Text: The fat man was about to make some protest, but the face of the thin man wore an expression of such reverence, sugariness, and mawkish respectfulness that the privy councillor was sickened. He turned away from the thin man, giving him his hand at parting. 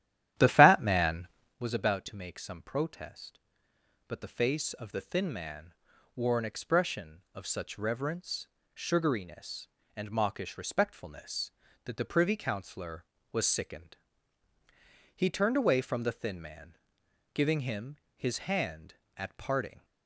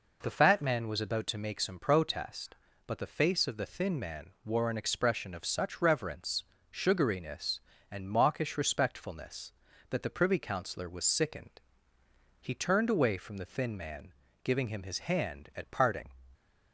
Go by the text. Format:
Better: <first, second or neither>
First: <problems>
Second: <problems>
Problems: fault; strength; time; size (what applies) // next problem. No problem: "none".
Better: second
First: starts louder than the rest; strong; until 1.6 s; 12 dB // pauses between "man" and "wore"; at 5.7 s; 0.44 s long // pauses between "him" and "his"; slight; at 17.9 s; 0.22 s long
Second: pauses between "man" and "wore"; slight; at 4.2 s; 0.16 s long